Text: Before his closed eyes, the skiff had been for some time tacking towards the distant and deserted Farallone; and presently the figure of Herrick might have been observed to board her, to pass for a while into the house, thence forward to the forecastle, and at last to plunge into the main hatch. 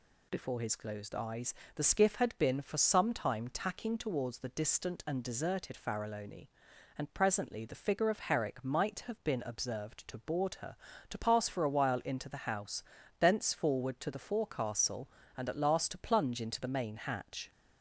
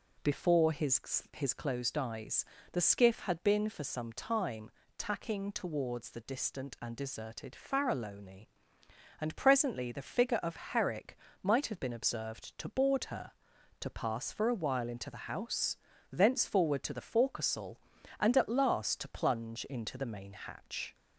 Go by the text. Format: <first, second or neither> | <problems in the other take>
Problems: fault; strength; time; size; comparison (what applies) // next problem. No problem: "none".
first | says "his" twice; at 1.3 s // pauses between "time" and "tacking"; slight; at 4.6 s; 0.28 s long // pauses between "Herrick" and "might"; slight; at 11.1 s; 0.24 s long